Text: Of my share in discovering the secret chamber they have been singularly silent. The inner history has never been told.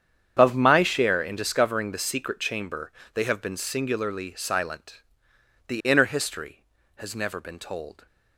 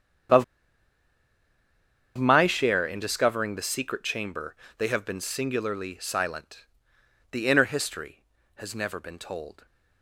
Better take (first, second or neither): first